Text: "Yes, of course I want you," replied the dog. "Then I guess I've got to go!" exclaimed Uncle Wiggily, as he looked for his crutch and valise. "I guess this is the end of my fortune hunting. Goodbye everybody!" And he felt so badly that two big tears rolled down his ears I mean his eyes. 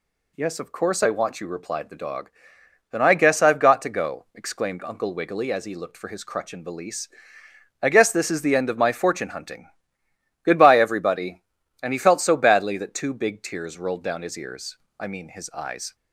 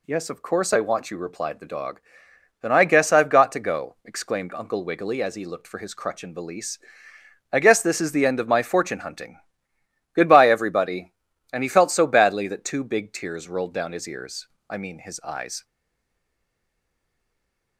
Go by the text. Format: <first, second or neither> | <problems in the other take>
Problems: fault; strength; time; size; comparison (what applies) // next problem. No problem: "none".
first | pauses between "ears" and "I"; slight; at 14.4 s; 0.20 s long; slight in the first // stays silent after the last word; from 15.6 s on; 2.1 s long